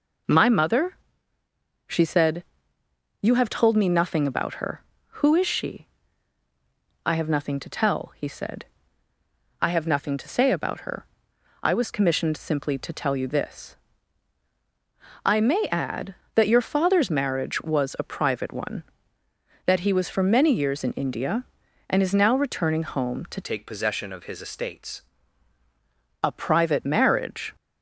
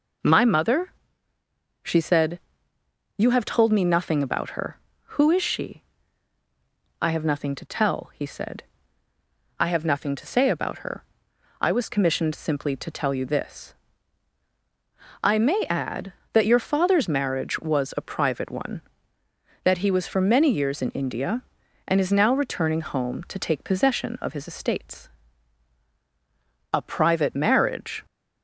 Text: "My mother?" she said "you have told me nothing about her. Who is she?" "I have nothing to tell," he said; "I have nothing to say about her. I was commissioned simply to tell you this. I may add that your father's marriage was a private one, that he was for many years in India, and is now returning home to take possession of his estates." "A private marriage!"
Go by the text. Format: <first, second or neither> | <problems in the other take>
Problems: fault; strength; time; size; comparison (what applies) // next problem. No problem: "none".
second | pauses between "said" and "you"; noticeable; at 2.4 s; 0.78 s long; noticeable in the second // changes voice from "take" to "estates"; from 23.4 to 25.0 s; 1.6 s long